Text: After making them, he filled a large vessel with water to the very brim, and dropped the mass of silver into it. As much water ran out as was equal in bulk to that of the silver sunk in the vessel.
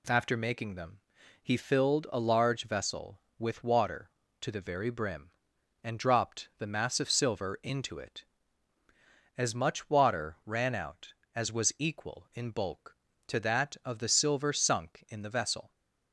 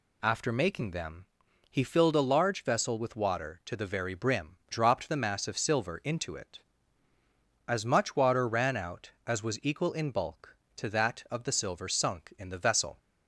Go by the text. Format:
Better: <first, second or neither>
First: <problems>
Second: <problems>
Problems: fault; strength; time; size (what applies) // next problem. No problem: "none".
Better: first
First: none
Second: skips "and"; at 4.6 s